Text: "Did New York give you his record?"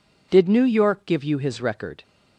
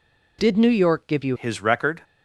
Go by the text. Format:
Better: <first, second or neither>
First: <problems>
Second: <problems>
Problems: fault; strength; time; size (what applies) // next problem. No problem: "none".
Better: first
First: none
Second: changes voice at "his"; from 1.3 s on; 0.7 s long